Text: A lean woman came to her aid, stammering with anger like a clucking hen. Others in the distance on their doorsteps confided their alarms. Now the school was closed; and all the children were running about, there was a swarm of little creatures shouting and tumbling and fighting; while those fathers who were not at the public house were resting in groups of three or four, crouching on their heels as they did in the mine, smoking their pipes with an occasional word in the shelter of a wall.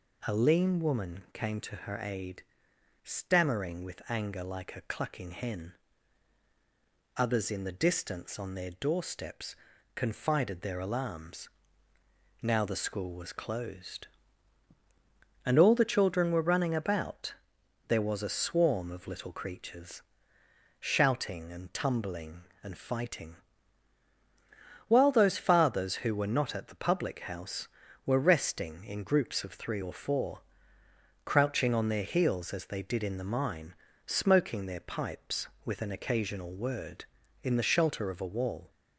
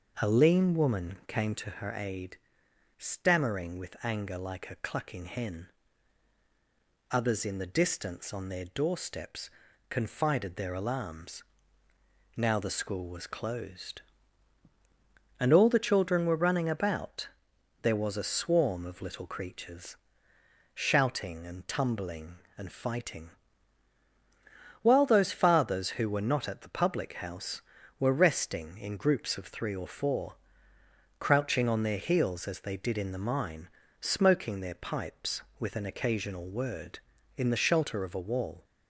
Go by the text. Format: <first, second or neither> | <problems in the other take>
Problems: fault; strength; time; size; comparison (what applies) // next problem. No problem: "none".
first | starts louder than the rest; noticeable; until 1.8 s; 5.5 dB // pauses between "doorsteps" and "confided"; at 9.4 s; 0.40 s long; also in the first // pauses between "creatures" and "shouting"; noticeable; at 19.9 s; 0.80 s long; noticeable in the first